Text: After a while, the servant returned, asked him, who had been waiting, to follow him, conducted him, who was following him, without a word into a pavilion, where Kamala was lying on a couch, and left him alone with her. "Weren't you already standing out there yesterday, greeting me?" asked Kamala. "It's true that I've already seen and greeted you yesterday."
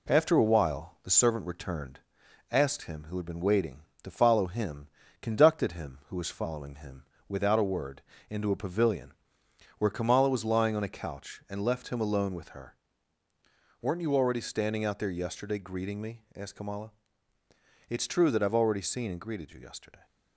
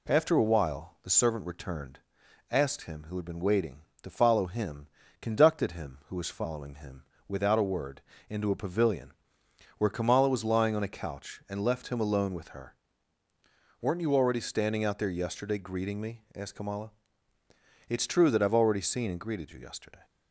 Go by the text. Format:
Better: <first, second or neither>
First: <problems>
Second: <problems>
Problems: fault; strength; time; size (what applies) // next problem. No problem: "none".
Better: second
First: gets quieter; slight; throughout; 3 dB // pauses between "word" and "into"; slight; at 8.0 s; 0.28 s long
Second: pauses between "word" and "into"; slight; at 8.0 s; 0.28 s long